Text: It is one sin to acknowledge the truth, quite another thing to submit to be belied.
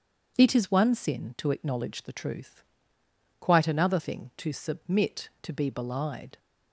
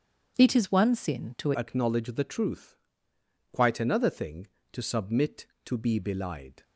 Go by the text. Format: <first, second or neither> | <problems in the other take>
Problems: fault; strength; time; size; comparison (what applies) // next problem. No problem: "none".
first | starts louder than the rest; strong; until 1.3 s; 7.5 dB; strong in the first // changes voice at "acknowledge"; from 1.5 s on; 5.1 s long